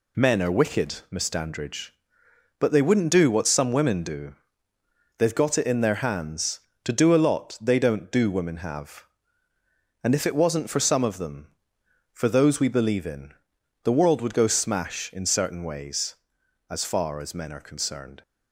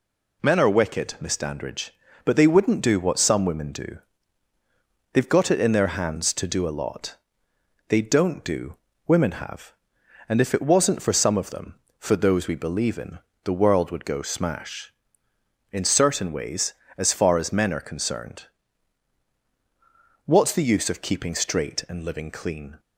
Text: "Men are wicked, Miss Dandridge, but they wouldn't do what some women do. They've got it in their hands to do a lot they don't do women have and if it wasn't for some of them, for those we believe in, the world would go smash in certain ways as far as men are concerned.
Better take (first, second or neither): first